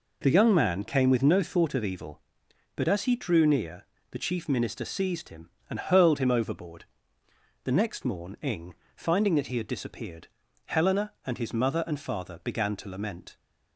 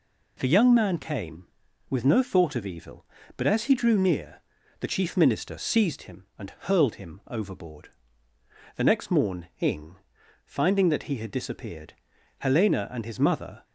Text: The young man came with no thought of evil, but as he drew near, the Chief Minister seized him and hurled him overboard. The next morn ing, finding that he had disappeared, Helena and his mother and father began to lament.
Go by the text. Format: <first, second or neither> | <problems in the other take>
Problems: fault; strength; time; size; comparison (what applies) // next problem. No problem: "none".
first | stops before "and father began to lament"; at 13.6 s